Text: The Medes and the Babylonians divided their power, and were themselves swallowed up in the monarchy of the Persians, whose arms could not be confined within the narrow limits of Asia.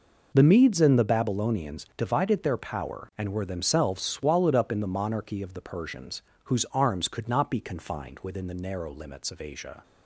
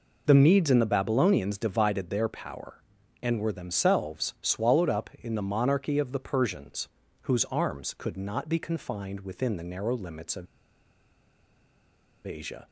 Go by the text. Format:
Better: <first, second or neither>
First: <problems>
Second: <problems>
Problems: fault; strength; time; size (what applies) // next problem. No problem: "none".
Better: first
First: none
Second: pauses between "of" and "Asia"; strong; at 10.4 s; 1.8 s long